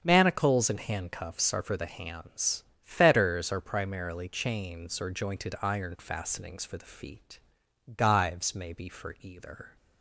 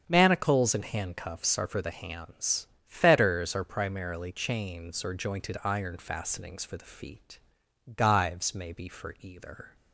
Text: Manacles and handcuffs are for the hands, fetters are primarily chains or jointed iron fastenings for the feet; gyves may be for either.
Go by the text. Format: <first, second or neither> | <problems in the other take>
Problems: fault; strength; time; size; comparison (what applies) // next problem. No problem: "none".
neither | starts louder than the rest; strong; the same in both